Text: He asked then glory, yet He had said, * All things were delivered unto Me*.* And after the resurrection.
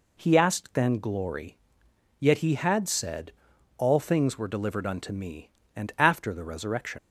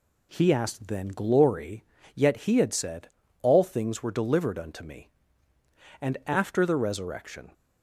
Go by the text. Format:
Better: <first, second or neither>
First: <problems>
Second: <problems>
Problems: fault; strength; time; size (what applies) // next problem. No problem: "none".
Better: second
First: leaves "resurrection" unfinished; at 6.9 s; 75 ms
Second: none